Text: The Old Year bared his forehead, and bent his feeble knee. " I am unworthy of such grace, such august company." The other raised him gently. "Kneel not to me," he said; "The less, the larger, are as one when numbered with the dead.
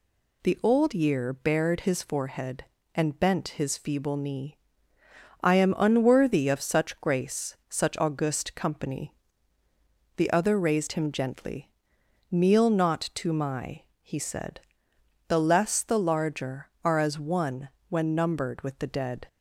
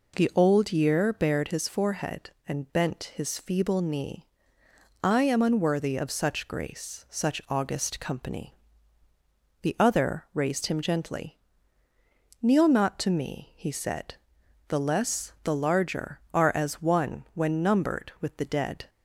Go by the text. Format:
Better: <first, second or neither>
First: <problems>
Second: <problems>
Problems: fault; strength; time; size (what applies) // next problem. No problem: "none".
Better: second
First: says "my" for "me"; at 13.3 s // pauses between "one" and "when"; slight; at 17.6 s; 0.20 s long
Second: none